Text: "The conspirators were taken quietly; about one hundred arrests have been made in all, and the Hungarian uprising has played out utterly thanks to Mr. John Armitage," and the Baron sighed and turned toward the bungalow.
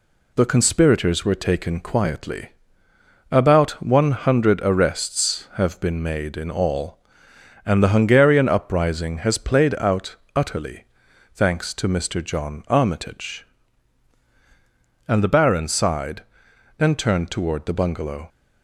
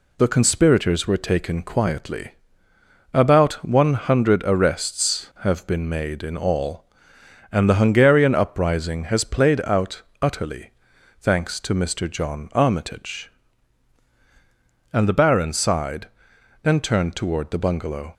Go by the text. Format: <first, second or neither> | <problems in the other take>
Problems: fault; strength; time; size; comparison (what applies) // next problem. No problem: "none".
neither | pauses between "out" and "utterly"; slight; the same in both // pauses between "utterly" and "thanks"; noticeable; the same in both